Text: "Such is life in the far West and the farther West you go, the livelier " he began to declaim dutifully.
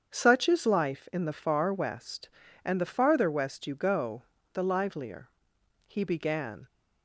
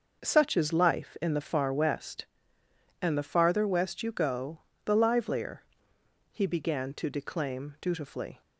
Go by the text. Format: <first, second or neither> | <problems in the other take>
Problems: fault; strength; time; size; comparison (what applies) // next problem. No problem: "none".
second | starts louder than the rest; strong; until 1.1 s; 8 dB; also in the second // stops before "to declaim dutifully"; at 6.6 s